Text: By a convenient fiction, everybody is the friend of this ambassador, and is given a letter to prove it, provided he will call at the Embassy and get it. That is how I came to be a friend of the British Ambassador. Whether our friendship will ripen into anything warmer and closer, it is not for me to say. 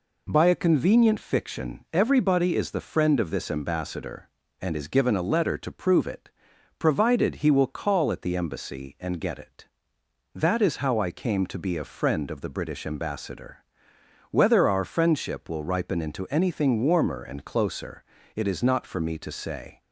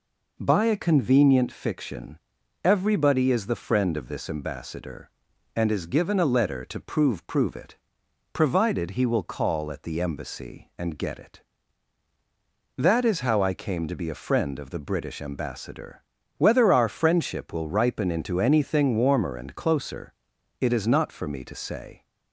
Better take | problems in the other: first | says "prove" twice; at 7.2 s

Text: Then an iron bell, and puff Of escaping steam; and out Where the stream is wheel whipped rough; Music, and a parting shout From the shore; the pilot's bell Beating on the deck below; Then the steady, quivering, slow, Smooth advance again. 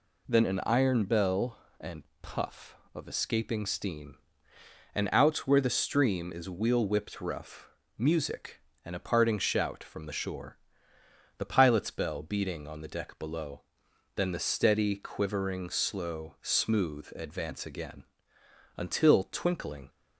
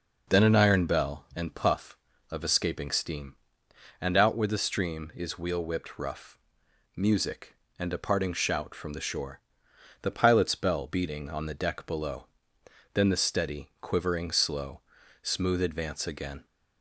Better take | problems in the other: second | pauses between "and" and "puff"; slight; at 2.0 s; 0.18 s long // goes on to say "Until Twinkling"; noticeable; from 18.7 s on; 1.1 s long

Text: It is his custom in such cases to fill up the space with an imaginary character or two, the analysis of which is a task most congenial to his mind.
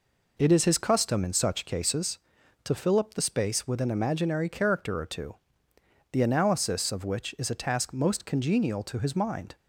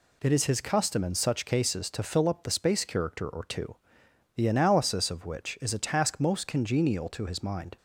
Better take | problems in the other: first | skips "with an imaginary"; at 2.8 s

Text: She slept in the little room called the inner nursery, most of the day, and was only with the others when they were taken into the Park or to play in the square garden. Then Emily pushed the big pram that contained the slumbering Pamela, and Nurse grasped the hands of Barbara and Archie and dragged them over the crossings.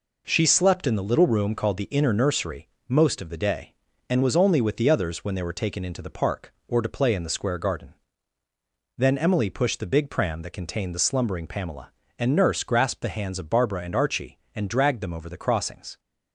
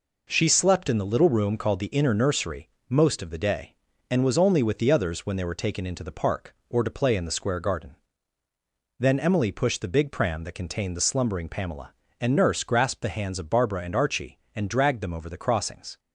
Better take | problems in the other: neither | none

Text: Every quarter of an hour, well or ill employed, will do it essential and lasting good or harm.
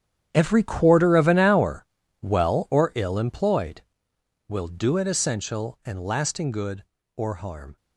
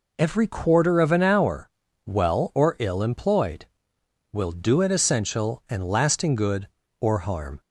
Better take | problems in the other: second | gets quieter; strong; throughout; 15 dB

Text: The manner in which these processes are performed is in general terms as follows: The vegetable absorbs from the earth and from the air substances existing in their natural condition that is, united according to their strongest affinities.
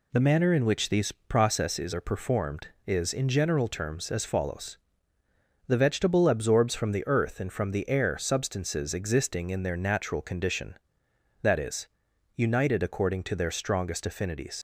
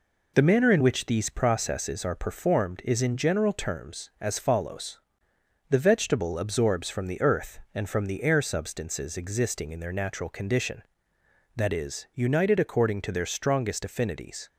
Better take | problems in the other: second | leaves "affinities" unfinished; at 14.5 s; 70 ms

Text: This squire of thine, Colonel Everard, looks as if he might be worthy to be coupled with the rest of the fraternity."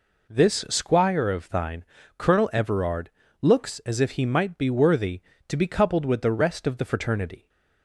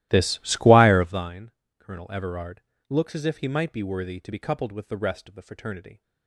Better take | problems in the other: first | starts louder than the rest; strong; until 1.3 s; 15.5 dB

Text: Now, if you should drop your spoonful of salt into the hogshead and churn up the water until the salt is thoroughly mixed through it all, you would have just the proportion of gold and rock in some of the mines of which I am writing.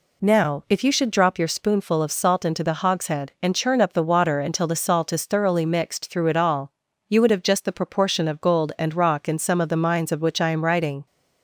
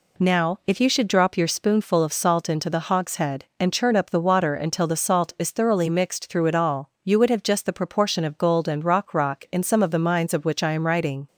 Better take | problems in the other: first | says "rock" twice; at 9.1 s

